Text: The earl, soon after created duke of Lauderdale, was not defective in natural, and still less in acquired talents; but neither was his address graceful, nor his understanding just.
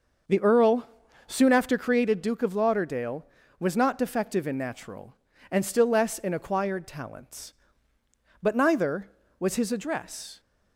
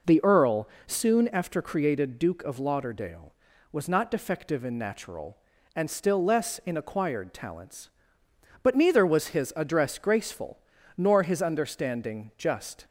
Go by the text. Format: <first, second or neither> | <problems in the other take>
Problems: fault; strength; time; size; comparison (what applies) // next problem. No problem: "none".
second | starts louder than the rest; noticeable; until 1.6 s; 6 dB // stops before "graceful nor his understanding just"; at 10.3 s